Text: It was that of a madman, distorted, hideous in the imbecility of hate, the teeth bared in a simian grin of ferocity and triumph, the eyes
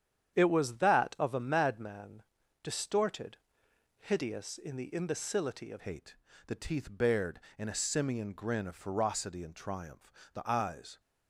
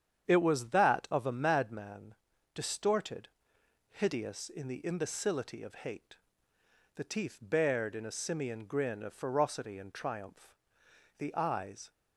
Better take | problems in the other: second | starts louder than the rest; strong; until 1.4 s; 9 dB; strong in the second // changes voice at "hate"; from 5.7 s on; 5.2 s long

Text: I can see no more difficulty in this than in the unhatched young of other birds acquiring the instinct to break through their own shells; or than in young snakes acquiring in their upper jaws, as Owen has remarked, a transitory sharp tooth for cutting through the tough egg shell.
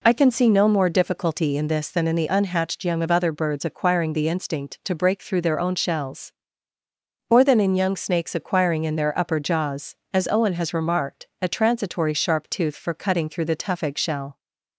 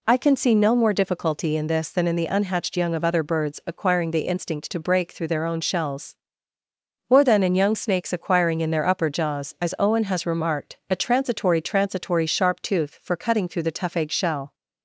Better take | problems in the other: first | says "transitory" twice; at 11.6 s

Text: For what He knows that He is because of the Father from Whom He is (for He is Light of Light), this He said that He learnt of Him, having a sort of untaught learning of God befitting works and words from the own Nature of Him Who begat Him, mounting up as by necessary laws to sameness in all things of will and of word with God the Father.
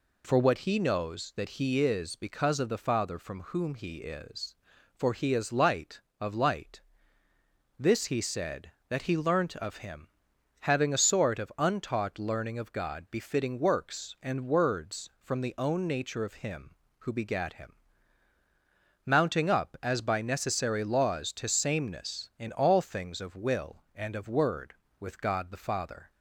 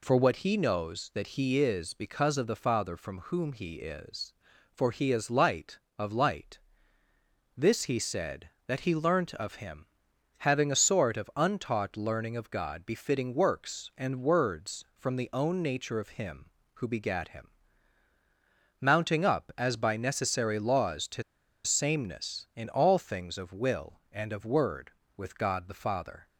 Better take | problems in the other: first | pauses between "to" and "sameness"; at 21.2 s; 0.42 s long

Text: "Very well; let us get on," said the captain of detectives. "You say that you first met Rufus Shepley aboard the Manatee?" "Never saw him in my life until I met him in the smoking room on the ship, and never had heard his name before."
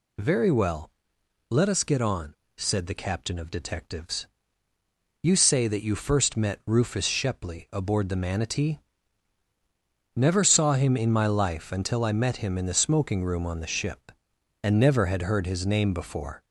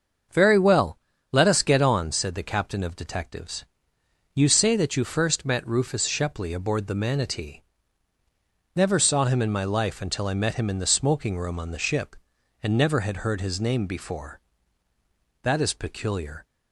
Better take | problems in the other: first | starts louder than the rest; until 1.6 s; 6.5 dB // goes on to say "That is peculiar"; noticeable; from 15.4 s on; 1.0 s long

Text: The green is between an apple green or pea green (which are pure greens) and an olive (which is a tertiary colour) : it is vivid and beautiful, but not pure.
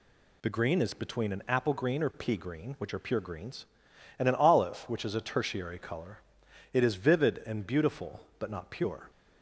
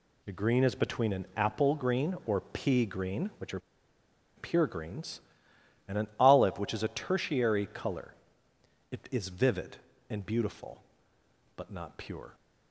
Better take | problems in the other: first | pauses between "are" and "pure"; noticeable; at 3.5 s; 0.77 s long

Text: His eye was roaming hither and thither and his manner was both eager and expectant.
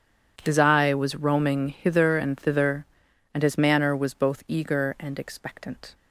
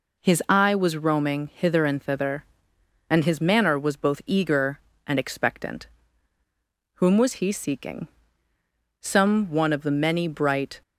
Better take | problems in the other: first | goes on to say "Whom was he seeking Some one of the many bright"; strong; from 6.9 s on; 3.8 s long

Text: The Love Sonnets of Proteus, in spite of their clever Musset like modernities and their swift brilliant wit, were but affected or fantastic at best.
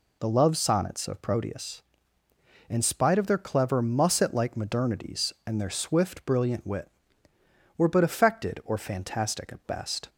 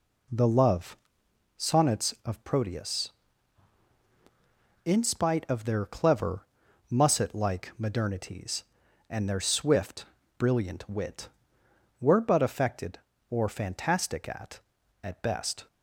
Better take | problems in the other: first | pauses between "Love" and "Sonnets"; noticeable; at 0.9 s; 0.58 s long // pauses between "clever" and "Musset"; noticeable; at 6.4 s; 0.46 s long // pauses between "swift" and "brilliant"; slight; at 10.0 s; 0.34 s long // says "at" twice; at 15.0 s

